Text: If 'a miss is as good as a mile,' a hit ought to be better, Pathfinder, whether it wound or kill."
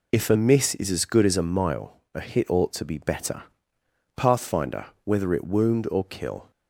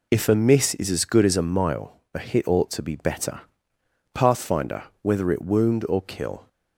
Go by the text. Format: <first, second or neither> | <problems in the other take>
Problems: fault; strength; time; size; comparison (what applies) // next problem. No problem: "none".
neither | none